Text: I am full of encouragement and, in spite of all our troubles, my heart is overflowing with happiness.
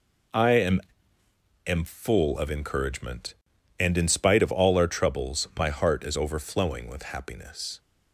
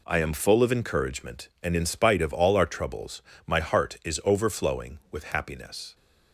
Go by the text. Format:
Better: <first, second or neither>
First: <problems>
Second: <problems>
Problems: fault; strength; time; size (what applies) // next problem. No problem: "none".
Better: second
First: says "am" twice; at 1.6 s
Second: none